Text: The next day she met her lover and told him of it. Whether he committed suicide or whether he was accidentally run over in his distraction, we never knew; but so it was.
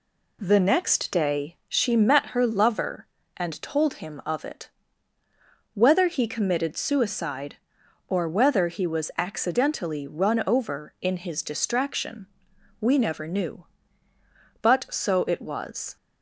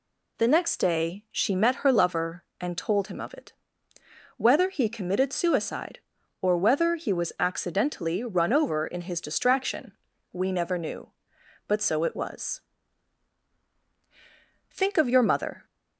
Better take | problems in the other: first | goes on to say "Think of your mother"; noticeable; from 14.6 s on; 0.96 s long

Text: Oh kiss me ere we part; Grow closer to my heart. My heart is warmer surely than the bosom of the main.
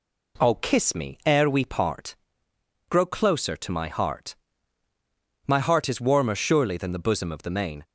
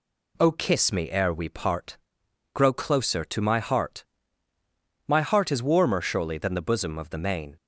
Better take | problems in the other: neither | none

